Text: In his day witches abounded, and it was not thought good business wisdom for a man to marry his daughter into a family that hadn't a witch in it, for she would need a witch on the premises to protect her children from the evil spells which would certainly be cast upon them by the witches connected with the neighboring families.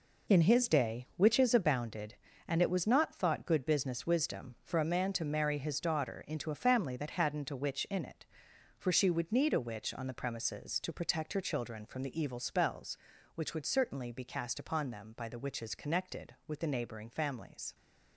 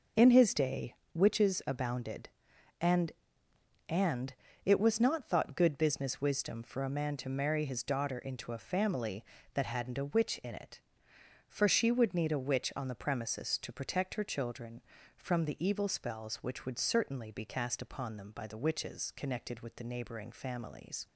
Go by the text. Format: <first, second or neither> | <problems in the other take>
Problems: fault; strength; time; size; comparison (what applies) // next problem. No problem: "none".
first | pauses between "day" and "witches"; slight; at 0.9 s; 0.20 s long // says "and" twice; at 3.8 s